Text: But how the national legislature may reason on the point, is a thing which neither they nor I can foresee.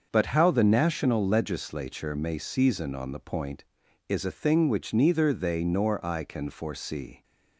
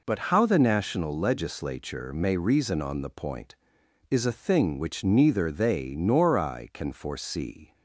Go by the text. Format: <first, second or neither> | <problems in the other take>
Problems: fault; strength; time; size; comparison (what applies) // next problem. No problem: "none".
second | starts louder than the rest; until 1.1 s; 6.5 dB // says "season" for "reason"; at 2.3 s